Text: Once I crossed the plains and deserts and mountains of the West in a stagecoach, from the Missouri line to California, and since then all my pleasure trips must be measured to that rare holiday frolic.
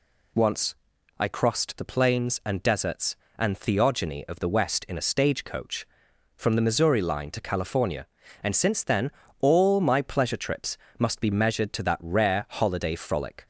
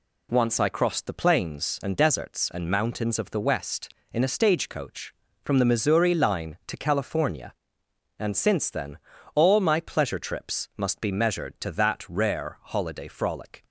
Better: second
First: pauses between "Once" and "I"; noticeable; at 0.7 s; 0.46 s long // says "theogony" for "mountains"; at 3.5 s // pauses between "then" and "all"; slight; at 9.1 s; 0.30 s long // pauses between "trips" and "must"; slight; at 10.7 s; 0.22 s long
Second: pauses between "then" and "all"; slight; at 8.9 s; 0.36 s long

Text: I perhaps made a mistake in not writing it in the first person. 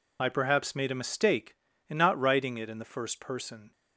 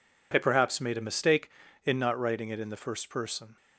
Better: second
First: loses the start of "I"; at 0.1 s; 35 ms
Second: none

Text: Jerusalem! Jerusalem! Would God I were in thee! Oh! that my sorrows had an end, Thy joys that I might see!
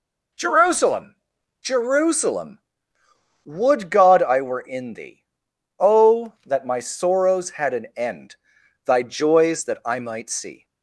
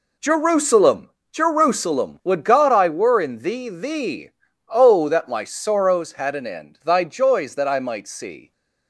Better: first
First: none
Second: says "thee" twice; at 3.6 s

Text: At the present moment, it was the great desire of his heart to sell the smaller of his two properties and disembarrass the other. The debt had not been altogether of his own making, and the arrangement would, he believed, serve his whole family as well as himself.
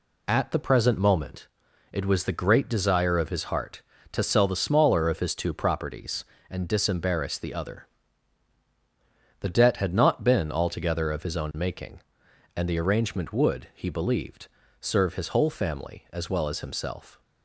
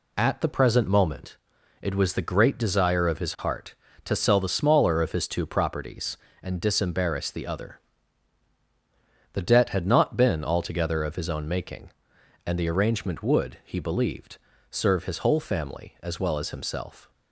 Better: neither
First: none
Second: none

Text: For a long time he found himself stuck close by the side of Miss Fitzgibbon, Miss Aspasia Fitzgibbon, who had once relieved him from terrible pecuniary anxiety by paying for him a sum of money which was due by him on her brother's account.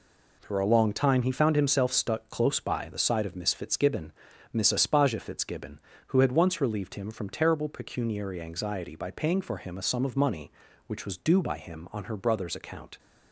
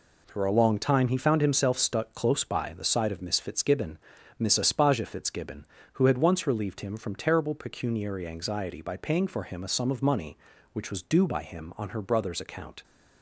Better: neither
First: none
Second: none

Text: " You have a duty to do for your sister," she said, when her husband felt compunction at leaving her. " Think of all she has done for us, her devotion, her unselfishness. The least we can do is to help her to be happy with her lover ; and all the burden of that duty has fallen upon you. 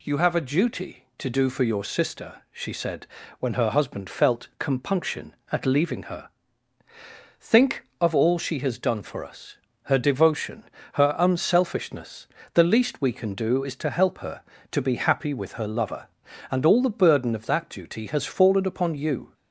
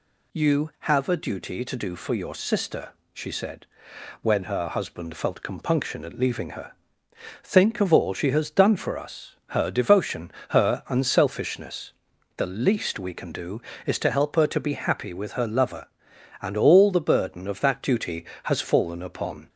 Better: first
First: none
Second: stops before "you"; at 19.4 s

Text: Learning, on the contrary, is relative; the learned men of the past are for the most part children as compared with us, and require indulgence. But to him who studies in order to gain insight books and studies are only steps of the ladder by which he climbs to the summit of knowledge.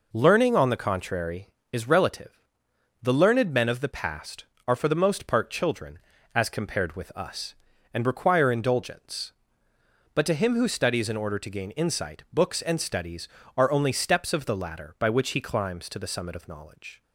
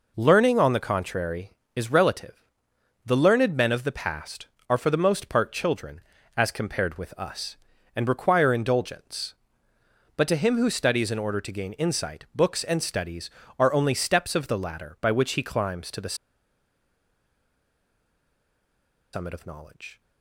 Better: first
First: none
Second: pauses between "the" and "summit"; strong; at 16.1 s; 2.9 s long

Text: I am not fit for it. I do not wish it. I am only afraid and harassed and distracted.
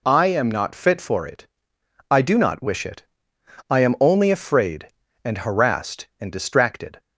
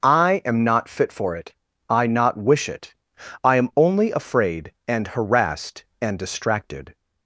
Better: first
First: none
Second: starts louder than the rest; noticeable; until 1.0 s; 6 dB // skips "do"; at 2.0 s

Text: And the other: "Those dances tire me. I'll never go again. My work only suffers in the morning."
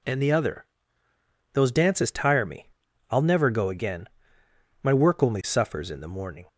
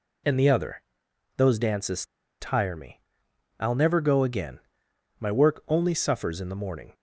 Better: first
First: none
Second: pauses between "dances" and "tire"; slight; at 2.0 s; 0.34 s long

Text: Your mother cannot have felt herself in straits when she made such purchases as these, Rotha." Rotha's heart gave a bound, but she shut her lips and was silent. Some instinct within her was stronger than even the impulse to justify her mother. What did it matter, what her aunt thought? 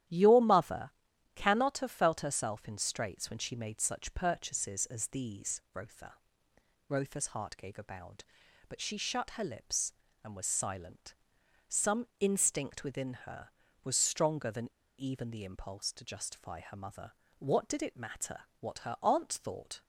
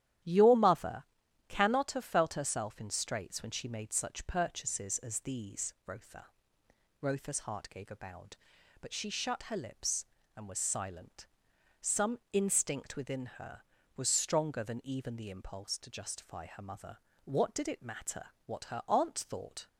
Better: second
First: starts louder than the rest; strong; until 1.5 s; 12 dB // pauses between "mother" and "cannot"; at 0.9 s; 0.44 s long // pauses between "Some" and "instinct"; slight; at 12.0 s; 0.16 s long // pauses between "than" and "even"; slight; at 14.7 s; 0.28 s long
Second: starts louder than the rest; strong; until 1.6 s; 11.5 dB // pauses between "mother" and "cannot"; at 1.0 s; 0.44 s long // pauses between "Some" and "instinct"; slight; at 12.1 s; 0.16 s long

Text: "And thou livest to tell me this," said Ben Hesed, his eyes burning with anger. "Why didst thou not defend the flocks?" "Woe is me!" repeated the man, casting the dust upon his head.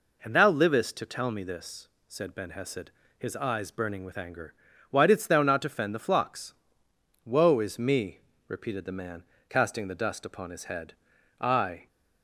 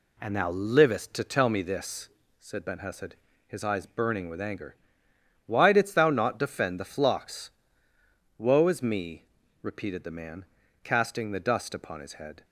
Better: second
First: goes on to say "I"; from 11.3 s on; 0.50 s long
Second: none

